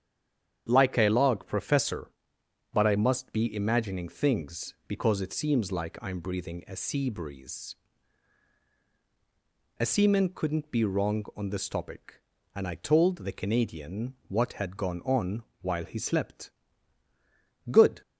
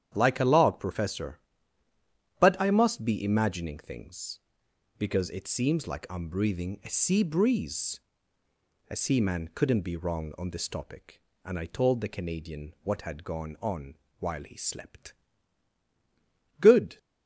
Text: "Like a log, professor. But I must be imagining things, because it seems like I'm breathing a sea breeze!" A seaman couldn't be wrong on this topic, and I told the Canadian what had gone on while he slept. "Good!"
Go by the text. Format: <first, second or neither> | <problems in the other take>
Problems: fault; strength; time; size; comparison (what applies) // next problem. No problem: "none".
second | stays silent before the first word; slight; until 0.6 s; 0.6 s long // starts louder than the rest; strong; until 1.7 s; 9 dB; strong in the second // pauses between "on" and "while"; slight; at 15.4 s; 0.18 s long; slight in the second